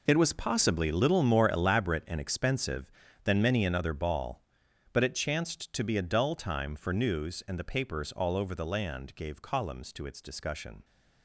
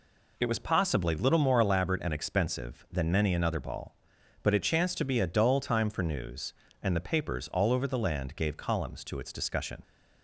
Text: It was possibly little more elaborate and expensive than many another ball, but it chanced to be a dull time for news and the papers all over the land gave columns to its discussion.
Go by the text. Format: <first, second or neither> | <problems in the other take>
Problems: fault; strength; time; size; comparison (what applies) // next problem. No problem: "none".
second | gets quieter; strong; throughout; 13.5 dB